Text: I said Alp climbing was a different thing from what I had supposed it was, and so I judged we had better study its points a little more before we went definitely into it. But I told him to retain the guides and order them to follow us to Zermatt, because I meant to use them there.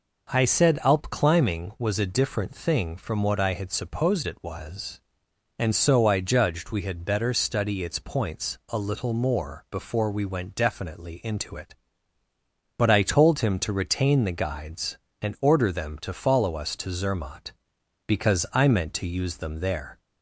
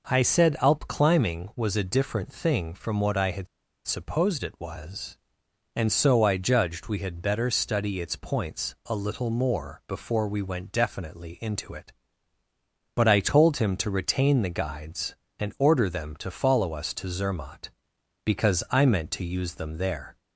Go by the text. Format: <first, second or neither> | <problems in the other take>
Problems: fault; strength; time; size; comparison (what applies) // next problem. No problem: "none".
first | pauses between "had" and "supposed"; at 3.4 s; 0.40 s long